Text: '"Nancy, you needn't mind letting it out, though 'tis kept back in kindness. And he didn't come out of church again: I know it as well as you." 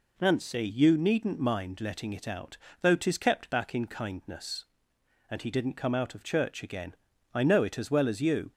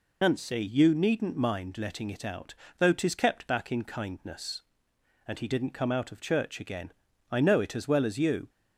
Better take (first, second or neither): first